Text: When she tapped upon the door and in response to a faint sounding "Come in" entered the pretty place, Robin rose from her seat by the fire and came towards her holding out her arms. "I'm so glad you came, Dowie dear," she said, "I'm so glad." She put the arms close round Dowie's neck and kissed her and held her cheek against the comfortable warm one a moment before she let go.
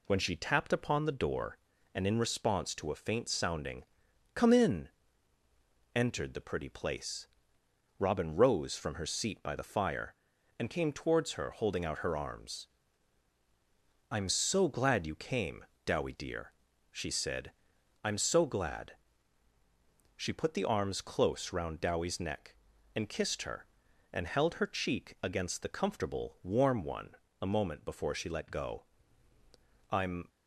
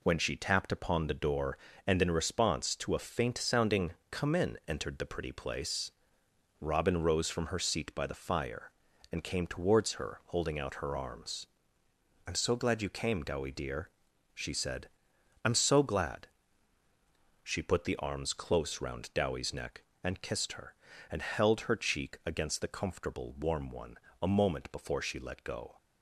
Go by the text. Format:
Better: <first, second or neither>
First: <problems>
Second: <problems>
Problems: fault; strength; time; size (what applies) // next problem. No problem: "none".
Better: second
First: pauses between "sounding" and "Come"; noticeable; at 3.8 s; 0.50 s long // pauses between "in" and "entered"; at 4.8 s; 1.0 s long // pauses between "one" and "a"; slight; at 27.1 s; 0.24 s long // goes on to say "I'm"; slight; from 29.8 s on; 0.38 s long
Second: pauses between "sounding" and "Come"; slight; at 3.9 s; 0.18 s long // pauses between "one" and "a"; slight; at 23.9 s; 0.22 s long